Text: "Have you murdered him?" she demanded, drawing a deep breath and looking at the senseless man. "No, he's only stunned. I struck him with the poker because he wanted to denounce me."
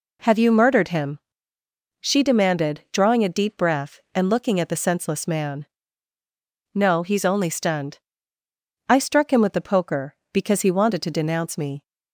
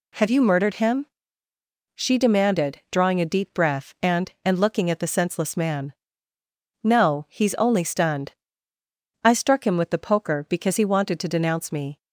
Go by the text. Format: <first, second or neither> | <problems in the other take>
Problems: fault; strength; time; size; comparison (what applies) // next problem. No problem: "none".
first | says "and" twice; at 4.4 s